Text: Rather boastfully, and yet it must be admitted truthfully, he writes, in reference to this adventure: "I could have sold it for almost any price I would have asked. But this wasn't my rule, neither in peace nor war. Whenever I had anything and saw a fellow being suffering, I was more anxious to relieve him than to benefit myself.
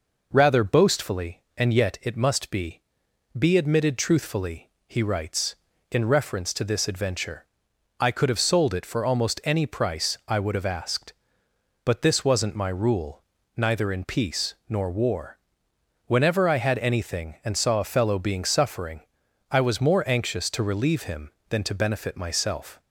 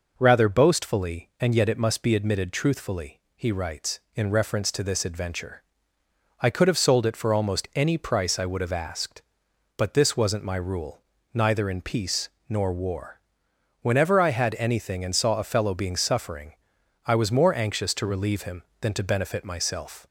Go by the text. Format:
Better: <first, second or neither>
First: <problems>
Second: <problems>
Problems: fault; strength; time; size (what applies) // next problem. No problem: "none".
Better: second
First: says "be" twice; at 3.3 s // pauses between "peace" and "nor"; slight; at 14.5 s; 0.16 s long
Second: pauses between "peace" and "nor"; slight; at 12.2 s; 0.18 s long